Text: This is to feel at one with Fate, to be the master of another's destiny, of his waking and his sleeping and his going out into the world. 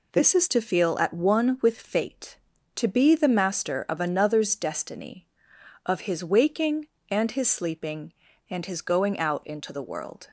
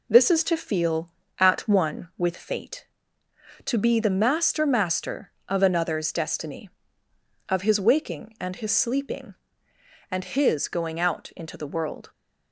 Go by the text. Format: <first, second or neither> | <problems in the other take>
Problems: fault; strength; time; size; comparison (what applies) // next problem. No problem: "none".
first | says "master" twice; at 4.6 s